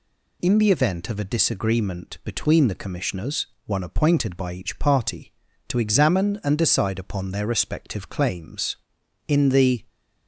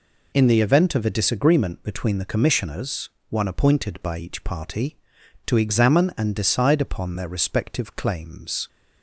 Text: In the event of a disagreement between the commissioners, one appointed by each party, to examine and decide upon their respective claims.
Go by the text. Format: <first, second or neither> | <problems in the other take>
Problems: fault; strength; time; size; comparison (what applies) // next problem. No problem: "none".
second | goes on to say "In the"; from 9.2 s on; 0.56 s long